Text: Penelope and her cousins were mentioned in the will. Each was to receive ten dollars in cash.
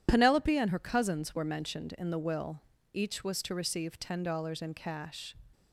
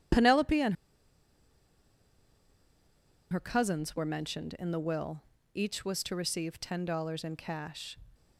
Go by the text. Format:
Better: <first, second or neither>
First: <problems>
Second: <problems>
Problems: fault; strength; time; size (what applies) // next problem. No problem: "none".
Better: first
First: none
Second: pauses between "and" and "her"; strong; at 0.7 s; 2.5 s long